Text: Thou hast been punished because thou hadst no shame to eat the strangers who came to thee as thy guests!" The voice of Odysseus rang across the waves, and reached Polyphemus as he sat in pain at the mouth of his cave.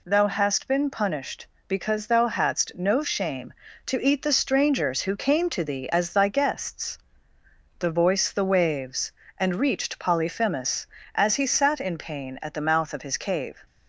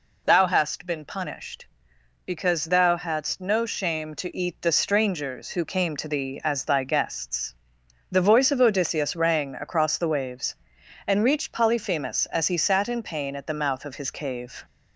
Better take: second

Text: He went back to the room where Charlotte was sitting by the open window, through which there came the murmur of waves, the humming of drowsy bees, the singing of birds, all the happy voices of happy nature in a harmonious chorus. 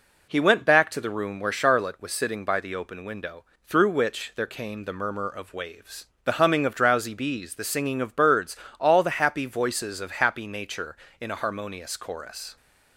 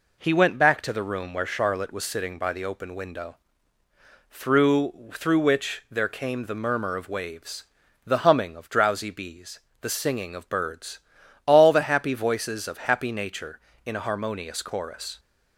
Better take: first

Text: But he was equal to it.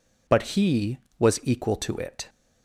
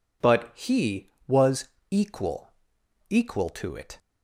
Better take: first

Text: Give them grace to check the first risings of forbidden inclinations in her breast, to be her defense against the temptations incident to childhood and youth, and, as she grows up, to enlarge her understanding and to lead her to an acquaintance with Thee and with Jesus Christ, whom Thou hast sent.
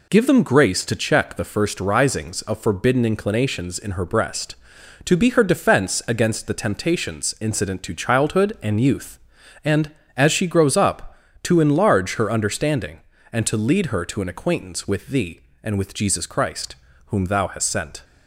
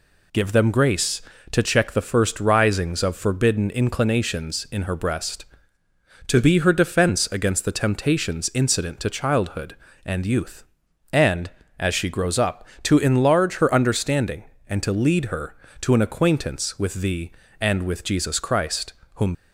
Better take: first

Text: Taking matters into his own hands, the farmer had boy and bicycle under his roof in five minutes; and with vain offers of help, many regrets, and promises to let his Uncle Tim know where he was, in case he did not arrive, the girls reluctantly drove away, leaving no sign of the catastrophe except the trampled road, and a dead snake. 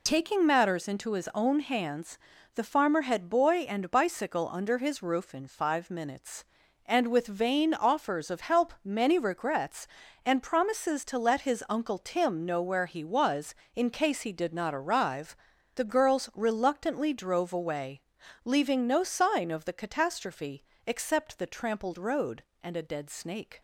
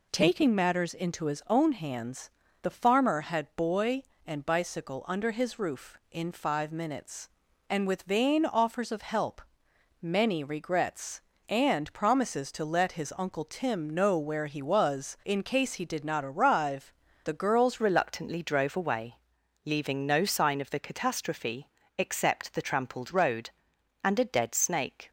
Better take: first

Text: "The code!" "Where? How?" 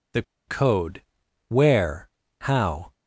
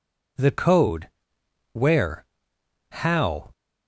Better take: second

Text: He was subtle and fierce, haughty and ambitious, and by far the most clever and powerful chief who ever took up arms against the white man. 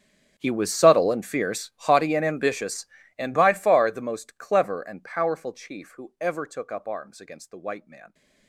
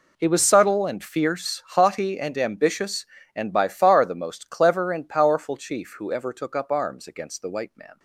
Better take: second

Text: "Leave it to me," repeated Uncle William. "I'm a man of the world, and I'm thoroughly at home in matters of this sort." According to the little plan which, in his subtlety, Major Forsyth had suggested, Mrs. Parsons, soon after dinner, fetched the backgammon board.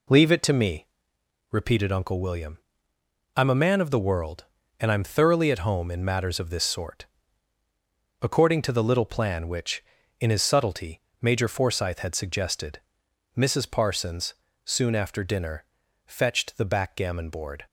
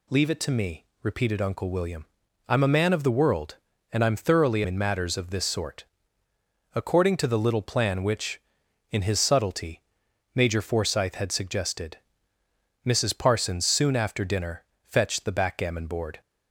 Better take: first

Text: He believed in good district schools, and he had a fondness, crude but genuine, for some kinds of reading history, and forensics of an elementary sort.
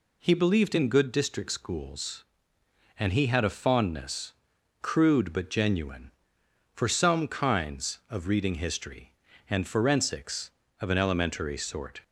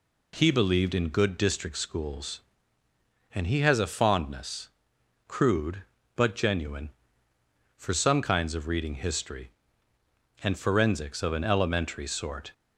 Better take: first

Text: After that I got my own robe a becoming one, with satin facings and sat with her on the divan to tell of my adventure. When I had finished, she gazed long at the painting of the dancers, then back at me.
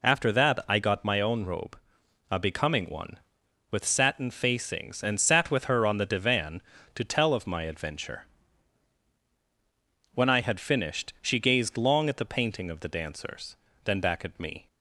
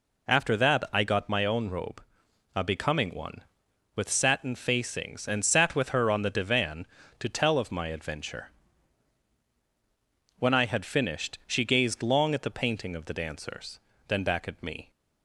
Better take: neither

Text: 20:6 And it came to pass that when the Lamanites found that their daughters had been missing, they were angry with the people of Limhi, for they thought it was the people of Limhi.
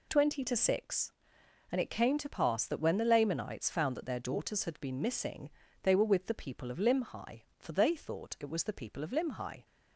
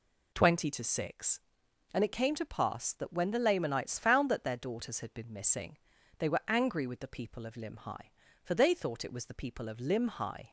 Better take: second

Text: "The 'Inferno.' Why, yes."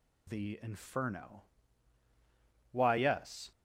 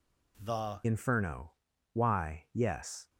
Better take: first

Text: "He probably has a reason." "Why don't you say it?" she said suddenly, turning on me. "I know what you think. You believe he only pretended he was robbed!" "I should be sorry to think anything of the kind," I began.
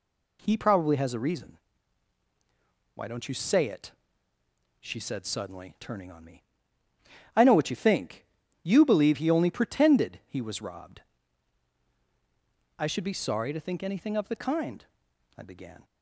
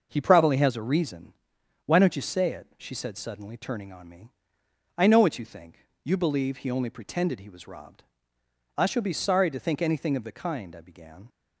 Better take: first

